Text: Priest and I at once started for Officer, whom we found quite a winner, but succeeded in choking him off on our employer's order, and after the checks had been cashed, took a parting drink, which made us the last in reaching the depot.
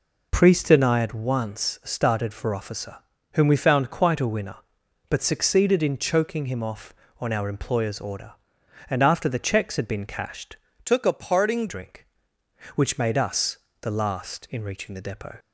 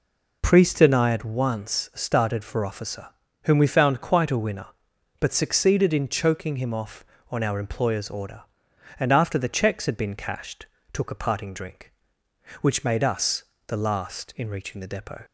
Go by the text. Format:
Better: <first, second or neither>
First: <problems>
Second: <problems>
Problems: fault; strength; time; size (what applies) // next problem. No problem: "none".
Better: second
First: changes voice from "took" to "parting"; from 10.8 to 11.6 s; 0.8 s long // pauses between "us" and "the"; slight; at 13.5 s; 0.22 s long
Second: pauses between "us" and "the"; slight; at 13.4 s; 0.22 s long